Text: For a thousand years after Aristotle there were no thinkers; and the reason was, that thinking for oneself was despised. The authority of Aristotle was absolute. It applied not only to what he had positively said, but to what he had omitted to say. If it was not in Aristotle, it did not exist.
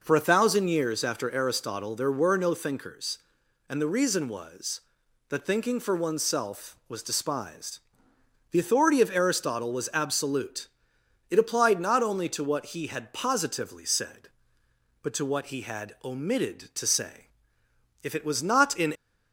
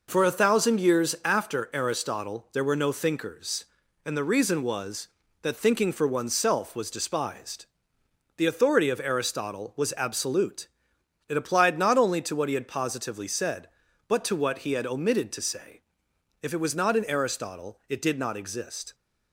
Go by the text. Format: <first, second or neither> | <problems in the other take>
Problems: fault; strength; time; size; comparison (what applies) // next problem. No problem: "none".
second | stops before "Aristotle it did not exist"; at 18.9 s